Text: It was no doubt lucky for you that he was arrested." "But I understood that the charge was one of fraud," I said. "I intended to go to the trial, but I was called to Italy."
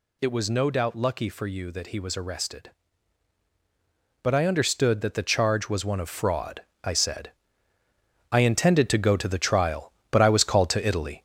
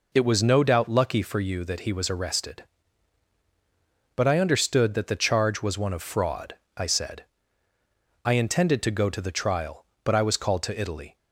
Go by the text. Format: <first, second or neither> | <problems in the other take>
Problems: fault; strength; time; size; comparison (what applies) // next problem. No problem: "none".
second | gets louder; noticeable; throughout; 5 dB